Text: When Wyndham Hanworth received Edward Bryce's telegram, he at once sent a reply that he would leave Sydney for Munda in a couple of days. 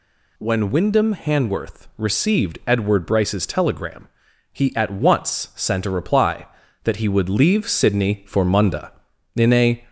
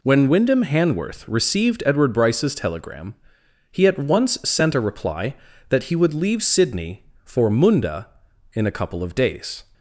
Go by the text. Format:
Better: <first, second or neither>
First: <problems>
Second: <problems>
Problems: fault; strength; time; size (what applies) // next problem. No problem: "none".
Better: second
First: stops before "couple of days"; at 9.8 s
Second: none